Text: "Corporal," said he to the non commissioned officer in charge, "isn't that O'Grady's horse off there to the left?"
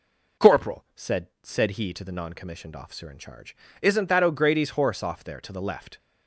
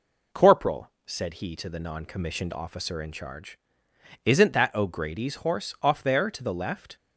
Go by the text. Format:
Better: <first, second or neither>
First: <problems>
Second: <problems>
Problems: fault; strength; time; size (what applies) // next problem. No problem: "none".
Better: second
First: says "said" twice; at 1.4 s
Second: none